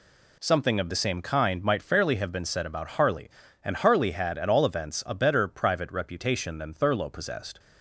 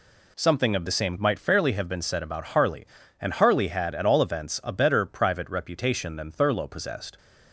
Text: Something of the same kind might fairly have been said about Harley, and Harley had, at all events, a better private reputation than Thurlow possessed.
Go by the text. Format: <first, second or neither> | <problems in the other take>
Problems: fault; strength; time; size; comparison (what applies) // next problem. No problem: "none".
first | skips "kind"; at 1.1 s